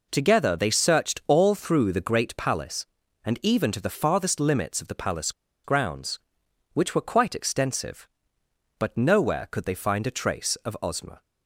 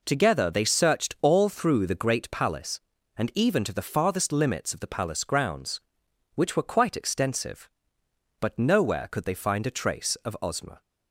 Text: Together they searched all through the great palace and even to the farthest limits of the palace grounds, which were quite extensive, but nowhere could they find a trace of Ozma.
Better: second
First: pauses between "palace" and "grounds"; slight; at 5.3 s; 0.31 s long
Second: none

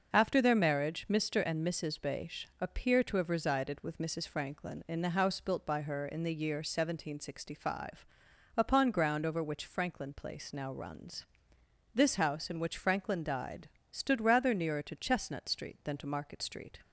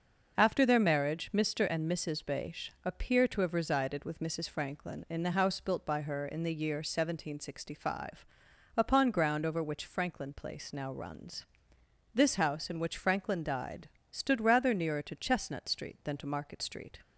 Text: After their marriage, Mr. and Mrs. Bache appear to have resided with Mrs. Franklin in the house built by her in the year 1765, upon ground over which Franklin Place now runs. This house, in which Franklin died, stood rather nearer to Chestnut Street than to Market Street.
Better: neither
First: starts louder than the rest; until 1.1 s; 6 dB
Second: starts louder than the rest; until 1.3 s; 6 dB

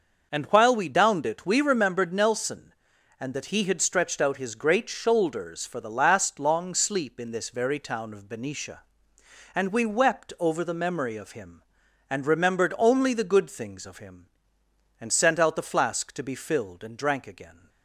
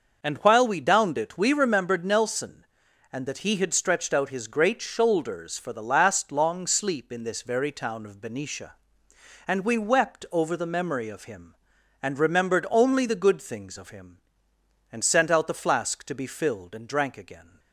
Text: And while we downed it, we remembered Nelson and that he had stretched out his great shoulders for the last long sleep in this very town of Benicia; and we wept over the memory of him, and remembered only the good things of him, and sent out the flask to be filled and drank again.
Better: neither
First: starts louder than the rest; noticeable; until 1.3 s; 6 dB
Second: starts louder than the rest; noticeable; until 1.2 s; 6 dB

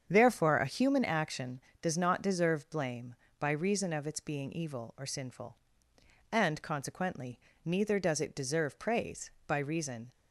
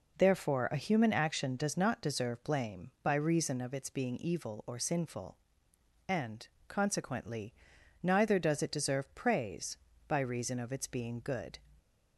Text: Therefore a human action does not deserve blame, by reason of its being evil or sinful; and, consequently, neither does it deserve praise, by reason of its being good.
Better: second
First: starts louder than the rest; strong; until 1.0 s; 7.5 dB // stops before "of its being good"; at 10.1 s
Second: none

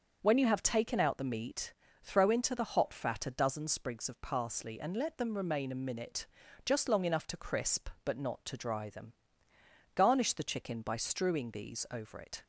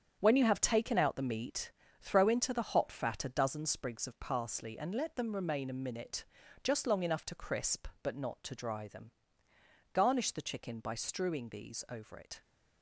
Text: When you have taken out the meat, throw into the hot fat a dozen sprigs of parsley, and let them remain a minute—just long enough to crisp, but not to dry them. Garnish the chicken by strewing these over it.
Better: first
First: starts louder than the rest; until 1.2 s; 6.5 dB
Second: gets quieter; strong; throughout; 9.5 dB // starts louder than the rest; strong; until 1.2 s; 8 dB

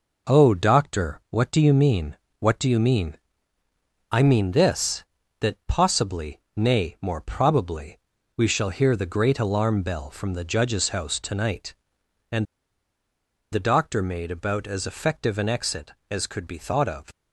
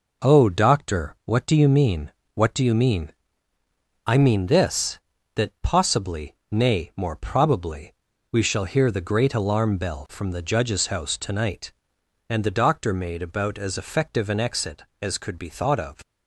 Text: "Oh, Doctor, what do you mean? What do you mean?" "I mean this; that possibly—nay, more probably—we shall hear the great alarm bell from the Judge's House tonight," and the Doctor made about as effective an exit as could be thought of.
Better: second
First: pauses between "and" and "the"; at 12.4 s; 1.0 s long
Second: none

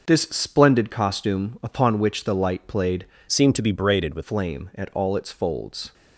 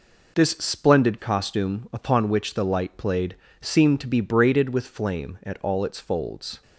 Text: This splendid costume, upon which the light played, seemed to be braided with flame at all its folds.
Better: second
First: changes voice from "seemed" to "with"; from 3.2 to 4.2 s; 1.0 s long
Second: none

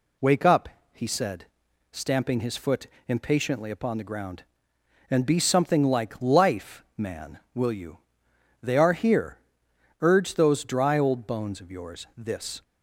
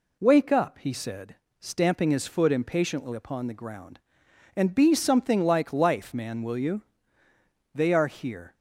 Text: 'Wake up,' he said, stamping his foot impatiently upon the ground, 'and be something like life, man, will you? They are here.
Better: second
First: pauses between "foot" and "impatiently"; slight; at 2.8 s; 0.20 s long // goes on to say "Urge those dry old bones of yours this"; strong; from 10.0 s on; 2.6 s long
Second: none

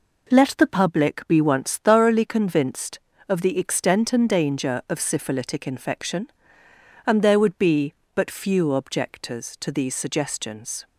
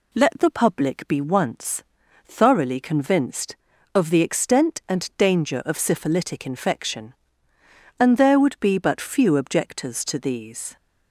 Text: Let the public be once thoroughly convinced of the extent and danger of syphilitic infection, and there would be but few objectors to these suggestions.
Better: first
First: none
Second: pauses between "once" and "thoroughly"; at 1.8 s; 0.42 s long // stops before "suggestions"; at 10.7 s

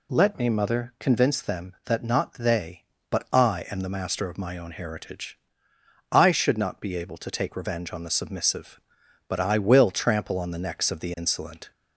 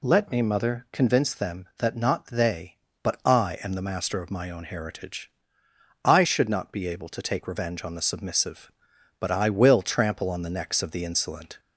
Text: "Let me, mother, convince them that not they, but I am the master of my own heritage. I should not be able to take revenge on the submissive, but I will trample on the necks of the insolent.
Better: neither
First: none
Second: none

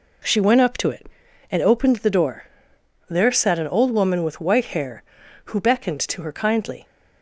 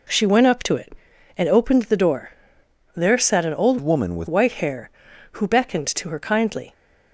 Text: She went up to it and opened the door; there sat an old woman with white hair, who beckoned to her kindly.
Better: first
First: none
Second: changes voice from "woman" to "with"; from 3.8 to 4.2 s; 0.4 s long

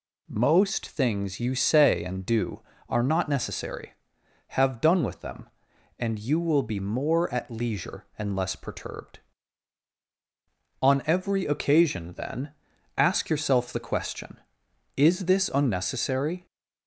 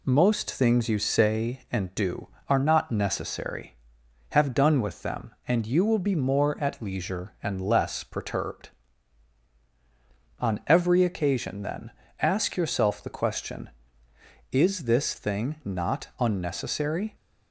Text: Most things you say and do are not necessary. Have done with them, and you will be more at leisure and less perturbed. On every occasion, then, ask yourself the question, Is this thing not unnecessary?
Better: second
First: skips "thing not"; at 15.5 s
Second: none

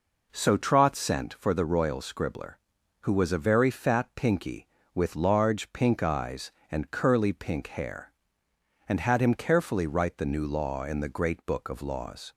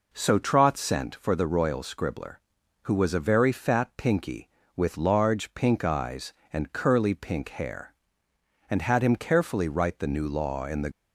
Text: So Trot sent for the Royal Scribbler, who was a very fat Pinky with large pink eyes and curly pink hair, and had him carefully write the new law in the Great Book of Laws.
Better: first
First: none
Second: stops before "Great Book of Laws"; at 10.9 s

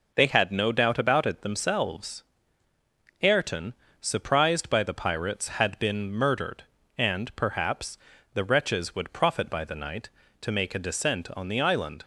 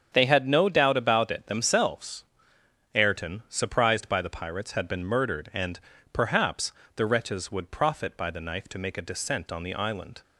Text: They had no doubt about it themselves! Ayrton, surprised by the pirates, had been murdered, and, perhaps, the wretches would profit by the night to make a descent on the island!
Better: first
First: none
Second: starts louder than the rest; strong; until 1.1 s; 7.5 dB // says "knife" for "night"; at 8.4 s

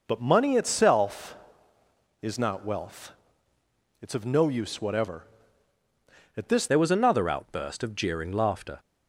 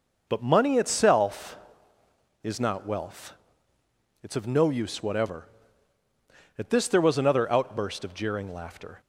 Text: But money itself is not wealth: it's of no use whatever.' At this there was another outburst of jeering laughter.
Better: second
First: changes voice at "there"; from 6.6 s on; 2.1 s long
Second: none

